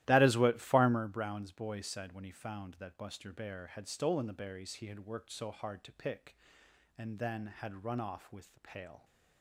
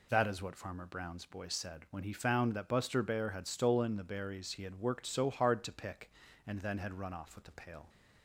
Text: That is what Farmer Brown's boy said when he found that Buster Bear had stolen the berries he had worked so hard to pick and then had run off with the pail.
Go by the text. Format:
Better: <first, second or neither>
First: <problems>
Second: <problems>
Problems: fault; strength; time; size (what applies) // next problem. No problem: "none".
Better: second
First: starts louder than the rest; strong; until 1.1 s; 14.5 dB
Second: none